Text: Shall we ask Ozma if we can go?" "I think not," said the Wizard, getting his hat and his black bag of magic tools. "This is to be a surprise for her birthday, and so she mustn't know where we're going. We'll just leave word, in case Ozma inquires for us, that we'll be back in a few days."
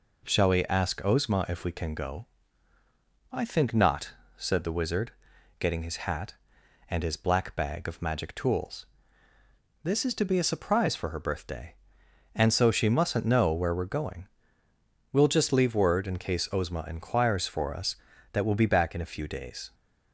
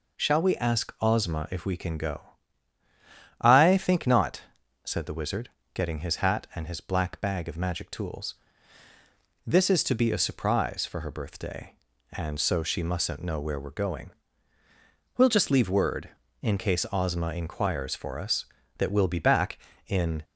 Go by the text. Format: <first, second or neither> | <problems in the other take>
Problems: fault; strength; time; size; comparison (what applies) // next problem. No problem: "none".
first | stops before "a few days"; at 20.2 s